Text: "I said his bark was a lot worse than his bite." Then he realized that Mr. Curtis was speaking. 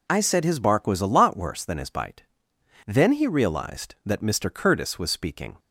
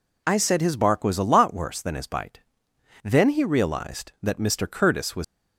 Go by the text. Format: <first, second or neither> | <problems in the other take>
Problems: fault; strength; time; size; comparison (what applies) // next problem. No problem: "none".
first | stops before "speaking"; at 5.2 s